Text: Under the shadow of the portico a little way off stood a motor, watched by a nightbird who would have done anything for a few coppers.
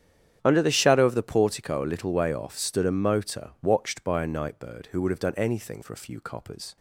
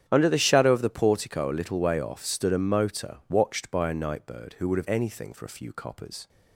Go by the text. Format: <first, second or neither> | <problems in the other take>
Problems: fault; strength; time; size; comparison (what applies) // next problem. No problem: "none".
first | starts louder than the rest; strong; until 1.0 s; 9.5 dB; strong in the first // skips "done"; at 4.8 s